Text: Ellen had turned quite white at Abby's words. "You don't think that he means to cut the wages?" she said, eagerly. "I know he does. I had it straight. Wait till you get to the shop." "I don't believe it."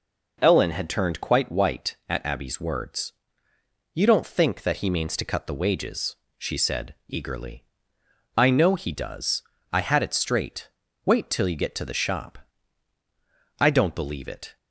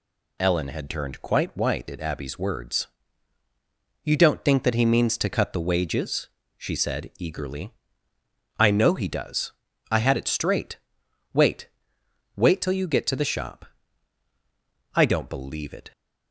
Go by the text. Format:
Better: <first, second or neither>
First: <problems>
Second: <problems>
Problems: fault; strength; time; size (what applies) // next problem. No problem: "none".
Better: first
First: none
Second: says "Wait" twice; at 12.3 s